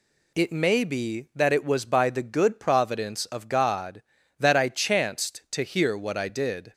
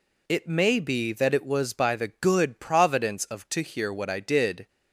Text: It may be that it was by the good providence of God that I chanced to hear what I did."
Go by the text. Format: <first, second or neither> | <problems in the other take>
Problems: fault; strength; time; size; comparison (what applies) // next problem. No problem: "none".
first | skips "God that I chanced"; at 3.4 s